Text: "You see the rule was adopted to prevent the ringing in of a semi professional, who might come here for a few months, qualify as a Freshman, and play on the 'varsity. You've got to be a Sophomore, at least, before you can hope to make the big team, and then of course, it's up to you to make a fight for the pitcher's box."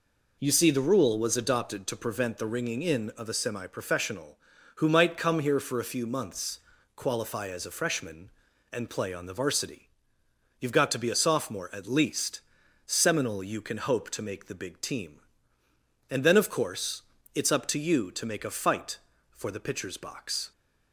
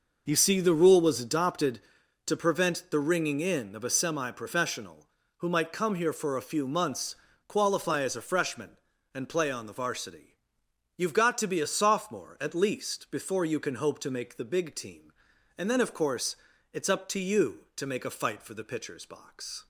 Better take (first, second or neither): second